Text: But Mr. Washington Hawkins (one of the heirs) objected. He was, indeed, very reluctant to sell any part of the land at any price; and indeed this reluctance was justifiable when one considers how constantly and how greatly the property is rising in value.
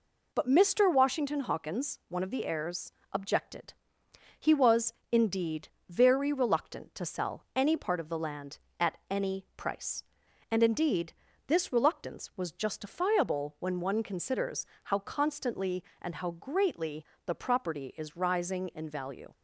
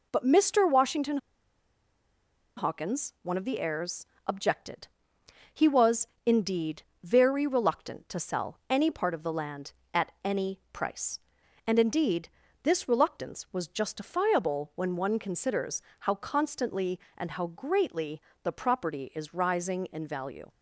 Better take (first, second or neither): first